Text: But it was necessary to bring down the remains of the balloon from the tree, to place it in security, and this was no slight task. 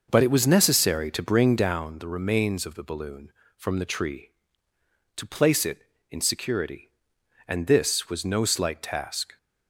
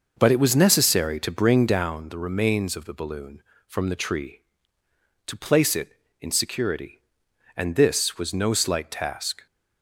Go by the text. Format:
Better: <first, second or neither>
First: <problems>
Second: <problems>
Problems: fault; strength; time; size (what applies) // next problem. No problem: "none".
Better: neither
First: none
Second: none